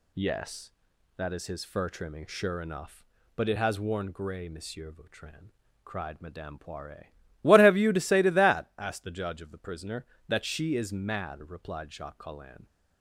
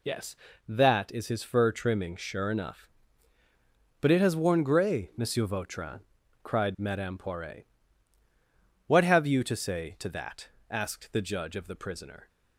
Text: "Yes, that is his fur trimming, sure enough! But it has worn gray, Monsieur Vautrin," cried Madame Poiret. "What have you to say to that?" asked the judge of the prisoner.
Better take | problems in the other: second | goes on to say "That she is mad replied Jacques Collin"; strong; from 10.2 s on; 2.3 s long

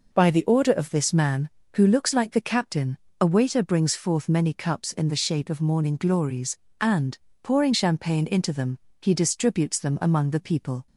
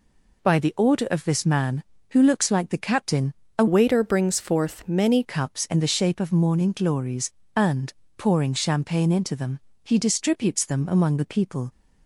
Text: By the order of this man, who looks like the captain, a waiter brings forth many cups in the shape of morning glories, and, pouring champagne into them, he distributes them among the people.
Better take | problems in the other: first | changes voice from "waiter" to "many"; from 3.6 to 5.2 s; 1.6 s long

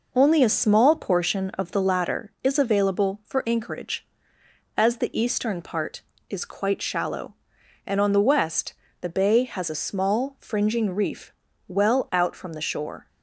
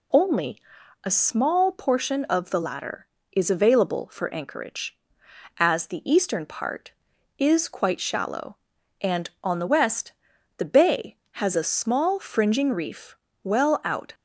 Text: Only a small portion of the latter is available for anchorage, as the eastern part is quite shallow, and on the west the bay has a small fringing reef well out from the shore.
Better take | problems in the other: first | pauses between "Only" and "a"; at 0.5 s; 0.44 s long // pauses between "west" and "the"; at 10.1 s; 0.44 s long; slight in the first // pauses between "reef" and "well"; slight; at 13.1 s; 0.28 s long; slight in the first // stops before "from the shore"; at 14.1 s

